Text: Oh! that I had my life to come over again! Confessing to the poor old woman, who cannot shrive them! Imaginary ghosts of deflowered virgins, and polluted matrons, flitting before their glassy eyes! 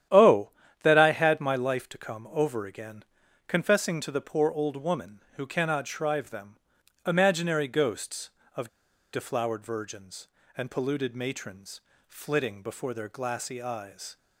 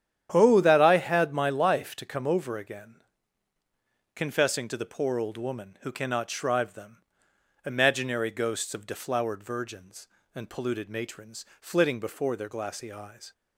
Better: second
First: starts louder than the rest; strong; until 1.4 s; 10 dB // pauses between "of" and "deflowered"; at 8.6 s; 0.45 s long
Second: starts louder than the rest; strong; until 1.3 s; 10 dB

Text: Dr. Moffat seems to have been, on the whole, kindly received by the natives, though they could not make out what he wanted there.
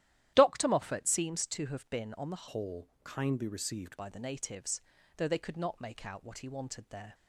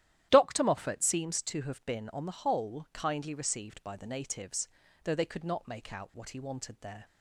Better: second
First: starts louder than the rest; strong; until 1.3 s; 12.5 dB // changes voice from "whole" to "received"; from 2.4 to 3.9 s; 1.5 s long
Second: starts louder than the rest; strong; until 1.3 s; 12 dB

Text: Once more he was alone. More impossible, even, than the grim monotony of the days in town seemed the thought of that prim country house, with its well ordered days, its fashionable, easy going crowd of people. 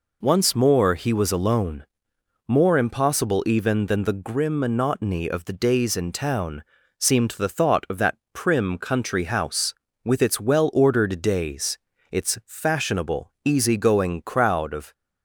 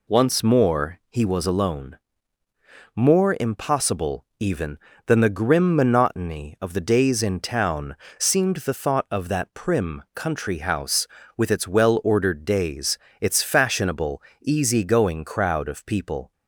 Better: second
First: pauses between "town" and "seemed"; slight; at 6.6 s; 0.36 s long // pauses between "that" and "prim"; slight; at 8.1 s; 0.18 s long // stops before "people"; at 14.9 s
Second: pauses between "town" and "seemed"; slight; at 7.9 s; 0.24 s long

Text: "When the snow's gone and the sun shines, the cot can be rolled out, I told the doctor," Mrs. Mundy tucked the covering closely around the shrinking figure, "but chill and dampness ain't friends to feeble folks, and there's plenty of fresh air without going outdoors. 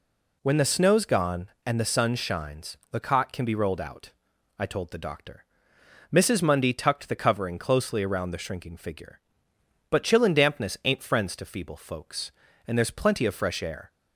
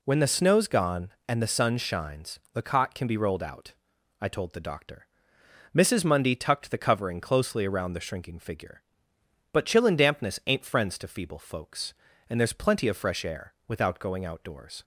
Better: second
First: stops before "without going outdoors"; at 13.9 s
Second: none

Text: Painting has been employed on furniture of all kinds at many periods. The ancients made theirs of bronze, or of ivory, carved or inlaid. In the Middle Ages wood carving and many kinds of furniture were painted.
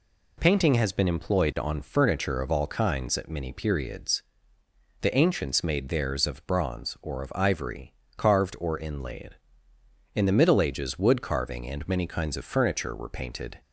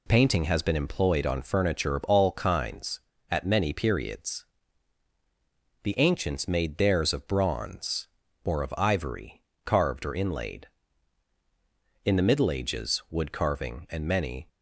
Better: first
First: none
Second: stops before "kinds of furniture were painted"; at 14.4 s

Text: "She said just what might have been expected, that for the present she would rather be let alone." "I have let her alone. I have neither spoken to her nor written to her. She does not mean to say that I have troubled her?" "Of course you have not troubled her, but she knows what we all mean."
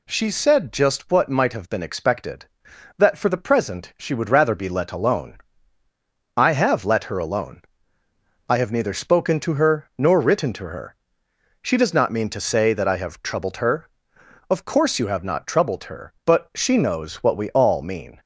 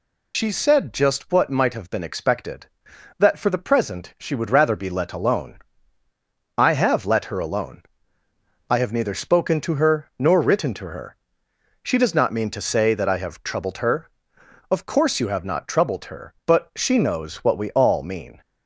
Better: first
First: none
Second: loses the start of "She"; at 0.3 s; 85 ms

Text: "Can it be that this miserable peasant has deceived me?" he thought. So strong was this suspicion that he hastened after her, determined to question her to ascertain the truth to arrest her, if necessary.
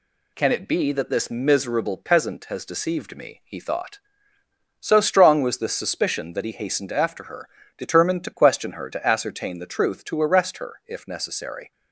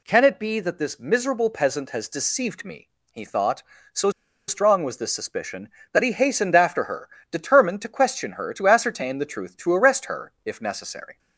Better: first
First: none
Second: pauses between "So" and "strong"; at 4.1 s; 0.37 s long

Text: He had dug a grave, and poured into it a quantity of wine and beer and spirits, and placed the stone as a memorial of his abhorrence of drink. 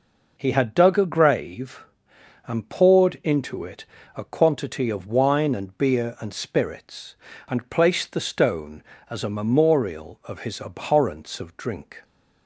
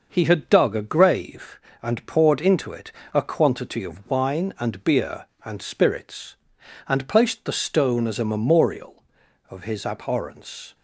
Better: first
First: pauses between "it" and "a"; slight; at 3.8 s; 0.30 s long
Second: starts louder than the rest; noticeable; until 1.1 s; 6 dB // pauses between "it" and "a"; slight; at 2.9 s; 0.22 s long // stops before "of drink"; at 10.7 s

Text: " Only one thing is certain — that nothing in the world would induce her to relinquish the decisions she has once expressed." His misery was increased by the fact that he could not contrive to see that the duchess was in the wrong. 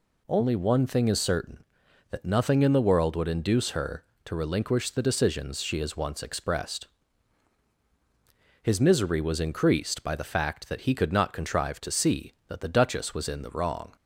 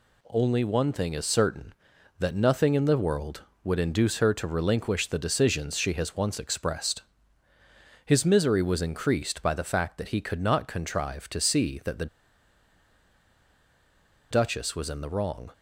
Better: first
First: none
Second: pauses between "the" and "duchess"; strong; at 12.0 s; 2.2 s long

